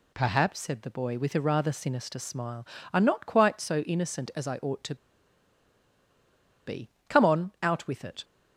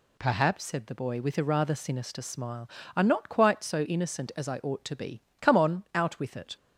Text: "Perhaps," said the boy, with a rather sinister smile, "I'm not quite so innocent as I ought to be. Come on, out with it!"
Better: second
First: pauses between "to" and "be"; strong; at 4.9 s; 1.7 s long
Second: none

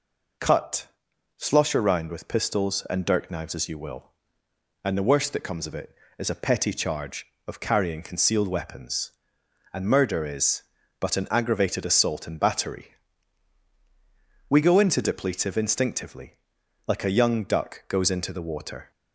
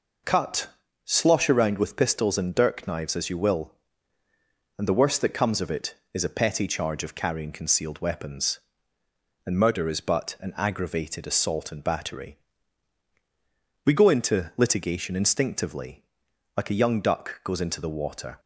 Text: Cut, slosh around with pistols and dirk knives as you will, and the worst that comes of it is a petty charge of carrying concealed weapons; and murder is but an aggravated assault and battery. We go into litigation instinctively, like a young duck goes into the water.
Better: second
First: says "depletive" for "litigation"; at 15.0 s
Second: none

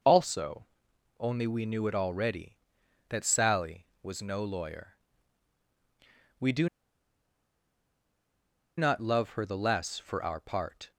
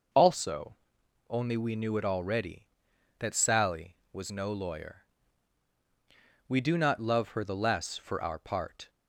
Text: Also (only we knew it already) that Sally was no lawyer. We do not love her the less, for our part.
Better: second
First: pauses between "do" and "not"; strong; at 6.6 s; 2.1 s long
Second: none

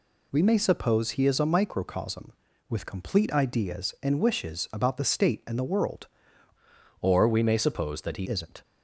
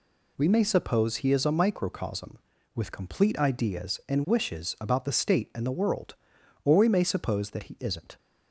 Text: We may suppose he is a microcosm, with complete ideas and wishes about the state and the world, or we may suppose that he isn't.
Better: second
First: changes voice from "or" to "he"; from 7.0 to 8.2 s; 1.2 s long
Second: none

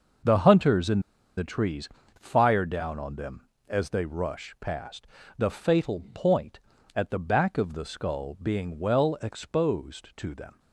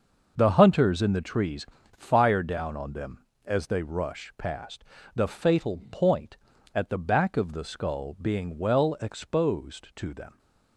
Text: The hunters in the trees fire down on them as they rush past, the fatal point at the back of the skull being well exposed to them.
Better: second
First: starts louder than the rest; noticeable; until 1.6 s; 6 dB // pauses between "in" and "the"; at 0.9 s; 0.37 s long // pauses between "trees" and "fire"; slight; at 1.8 s; 0.32 s long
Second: starts louder than the rest; noticeable; until 1.3 s; 6 dB // pauses between "trees" and "fire"; slight; at 1.6 s; 0.32 s long

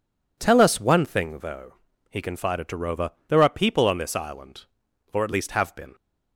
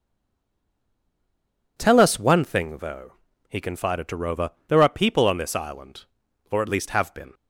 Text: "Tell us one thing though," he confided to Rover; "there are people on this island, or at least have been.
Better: first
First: none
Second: stays silent before the first word; noticeable; until 1.7 s; 1.7 s long

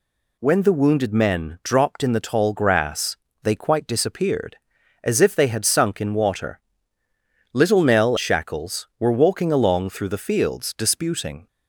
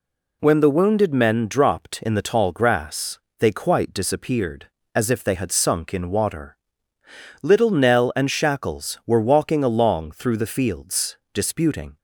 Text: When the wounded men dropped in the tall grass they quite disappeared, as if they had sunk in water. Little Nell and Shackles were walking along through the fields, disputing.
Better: second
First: pauses between "grass" and "they"; slight; at 3.1 s; 0.26 s long // skips "and"; at 8.1 s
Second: pauses between "grass" and "they"; slight; at 3.1 s; 0.22 s long

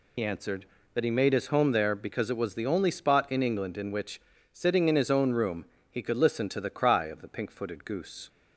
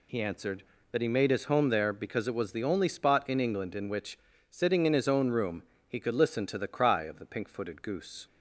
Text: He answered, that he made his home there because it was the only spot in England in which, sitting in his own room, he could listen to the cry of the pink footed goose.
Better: second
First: loses the start of "He"; at 0.1 s; 50 ms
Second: none

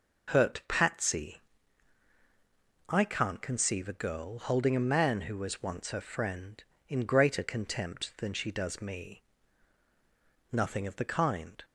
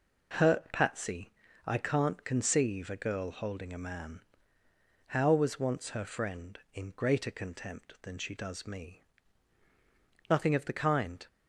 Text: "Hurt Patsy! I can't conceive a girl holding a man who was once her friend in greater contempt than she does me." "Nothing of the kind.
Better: first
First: none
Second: says "how" for "who"; at 5.0 s

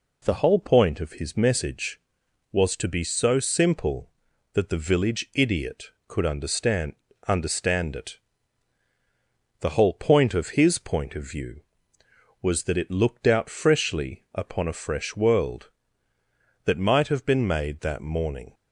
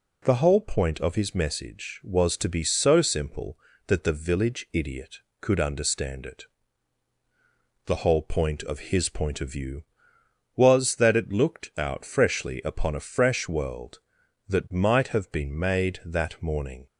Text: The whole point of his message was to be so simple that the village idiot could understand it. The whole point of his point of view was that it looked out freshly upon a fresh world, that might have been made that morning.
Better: second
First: says "understand" twice; at 7.2 s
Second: none

